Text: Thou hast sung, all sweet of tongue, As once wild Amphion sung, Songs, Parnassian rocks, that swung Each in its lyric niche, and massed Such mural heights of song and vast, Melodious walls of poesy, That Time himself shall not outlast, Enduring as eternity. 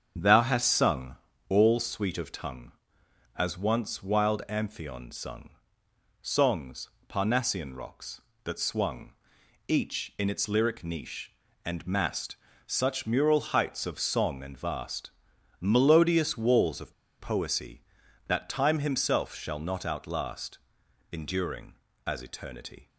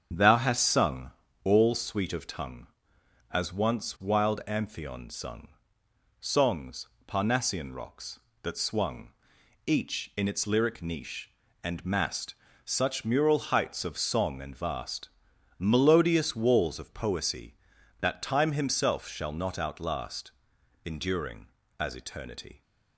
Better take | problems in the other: second | starts louder than the rest; strong; until 1.5 s; 7.5 dB; strong in the second // pauses between "swung" and "Each"; noticeable; at 9.1 s; 0.56 s long; noticeable in the second // pauses between "massed" and "Such"; slight; at 12.3 s; 0.30 s long; slight in the second // pauses between "of" and "poesy"; slight; at 16.9 s; 0.26 s long

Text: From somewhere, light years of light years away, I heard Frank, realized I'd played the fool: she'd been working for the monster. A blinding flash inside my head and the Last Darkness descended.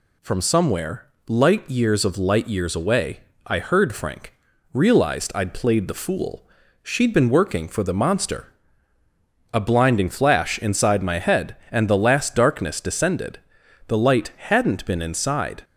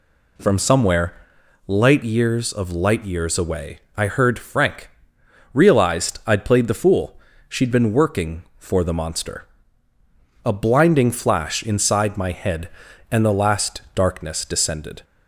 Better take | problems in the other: second | goes on to say "The light hadn't been inside"; strong; from 13.8 s on; 1.7 s long

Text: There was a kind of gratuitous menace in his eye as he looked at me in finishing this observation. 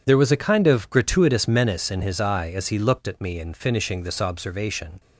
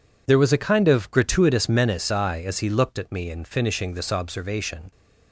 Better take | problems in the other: first | skips "in his"; at 2.1 s

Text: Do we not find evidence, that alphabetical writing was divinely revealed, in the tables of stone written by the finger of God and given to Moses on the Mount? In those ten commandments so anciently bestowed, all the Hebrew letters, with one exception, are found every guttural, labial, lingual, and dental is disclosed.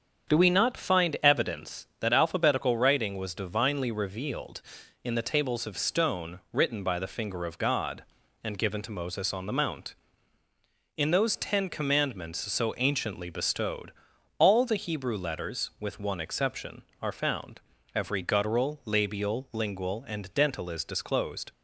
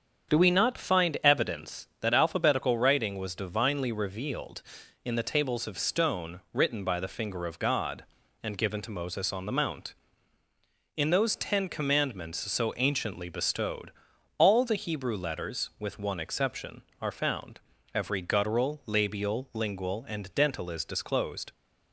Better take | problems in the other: neither | starts louder than the rest; strong; the same in both // pauses between "found" and "every"; slight; the same in both

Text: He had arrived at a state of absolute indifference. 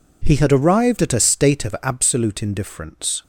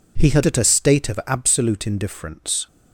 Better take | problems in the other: first | skips "arrived"; at 0.4 s

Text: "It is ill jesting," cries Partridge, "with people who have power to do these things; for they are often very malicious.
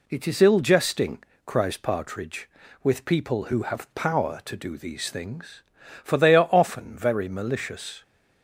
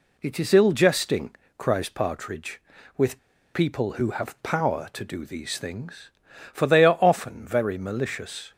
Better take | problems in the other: first | pauses between "with" and "people"; slight; at 3.1 s; 0.34 s long

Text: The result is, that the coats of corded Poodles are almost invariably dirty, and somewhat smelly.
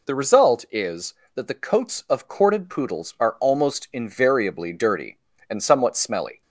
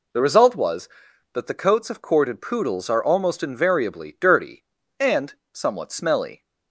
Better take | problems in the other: first | says "was" for "is"; at 0.5 s // pauses between "and" and "somewhat"; slight; at 5.3 s; 0.20 s long

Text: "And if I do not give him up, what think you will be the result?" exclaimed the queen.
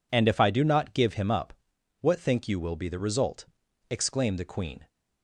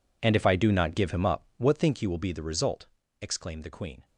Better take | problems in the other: first | gets quieter; strong; throughout; 18.5 dB

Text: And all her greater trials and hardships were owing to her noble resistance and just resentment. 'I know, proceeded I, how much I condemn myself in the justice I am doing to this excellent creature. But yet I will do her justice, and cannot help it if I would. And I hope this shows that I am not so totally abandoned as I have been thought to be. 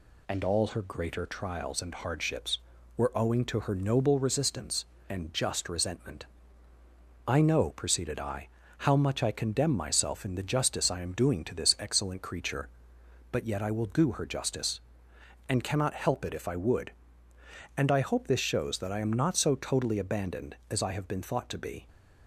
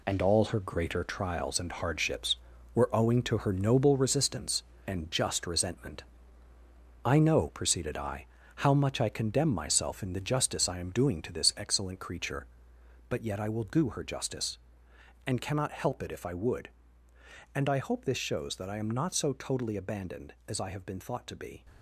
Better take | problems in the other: first | gets quieter; strong; throughout; 8.5 dB

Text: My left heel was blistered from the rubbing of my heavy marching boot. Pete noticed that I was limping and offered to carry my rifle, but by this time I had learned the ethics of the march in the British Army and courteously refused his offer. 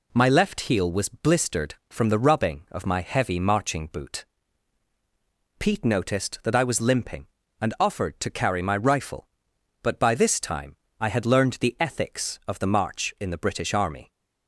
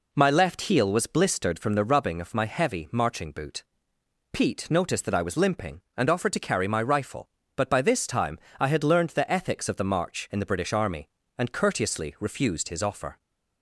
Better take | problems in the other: second | pauses between "time" and "I"; slight; at 10.7 s; 0.24 s long; slight in the second // stops before "and courteously refused his offer"; at 14.1 s

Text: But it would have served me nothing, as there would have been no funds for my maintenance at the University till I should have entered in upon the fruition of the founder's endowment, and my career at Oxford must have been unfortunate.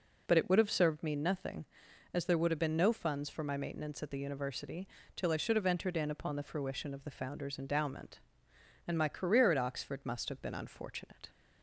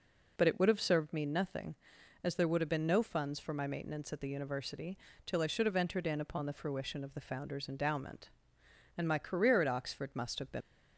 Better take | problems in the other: first | pauses between "University" and "till"; slight; at 4.9 s; 0.28 s long; slight in the first // stops before "unfortunate"; at 10.6 s

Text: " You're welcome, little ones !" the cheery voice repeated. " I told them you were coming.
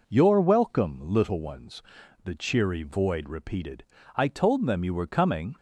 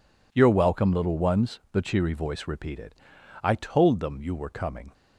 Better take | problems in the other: second | says "void" for "voice"; at 2.8 s

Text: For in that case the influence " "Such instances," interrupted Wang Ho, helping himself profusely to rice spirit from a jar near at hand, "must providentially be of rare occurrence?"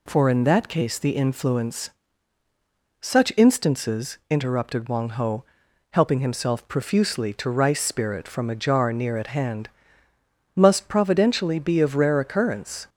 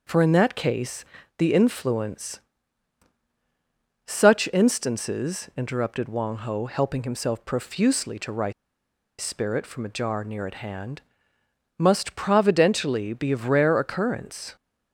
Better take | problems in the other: first | pauses between "case" and "the"; slight; at 1.0 s; 0.32 s long // pauses between "rice" and "spirit"; noticeable; at 8.5 s; 0.68 s long

